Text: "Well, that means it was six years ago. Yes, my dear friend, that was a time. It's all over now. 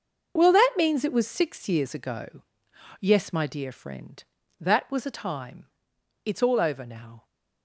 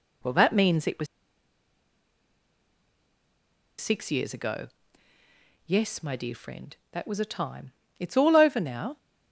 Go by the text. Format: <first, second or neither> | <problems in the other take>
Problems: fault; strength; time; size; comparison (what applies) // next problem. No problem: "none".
first | pauses between "was" and "six"; strong; at 1.0 s; 2.7 s long